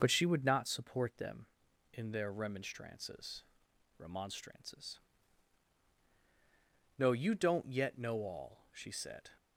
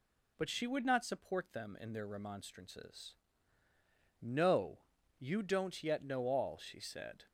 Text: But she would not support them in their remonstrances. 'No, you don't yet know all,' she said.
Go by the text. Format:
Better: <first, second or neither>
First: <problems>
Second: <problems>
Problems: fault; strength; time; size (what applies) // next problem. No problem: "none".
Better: second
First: says "remonstrances" twice; at 3.9 s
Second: none